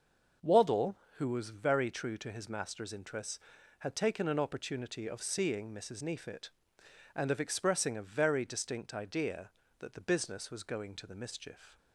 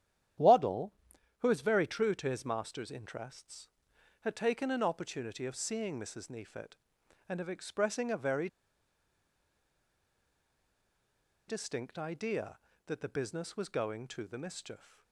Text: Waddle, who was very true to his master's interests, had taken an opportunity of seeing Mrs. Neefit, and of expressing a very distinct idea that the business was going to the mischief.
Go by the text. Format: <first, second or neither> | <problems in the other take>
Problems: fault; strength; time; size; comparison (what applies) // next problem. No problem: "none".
first | starts louder than the rest; strong; until 1.8 s; 10 dB; noticeable in the first // pauses between "very" and "distinct"; strong; at 8.4 s; 3.0 s long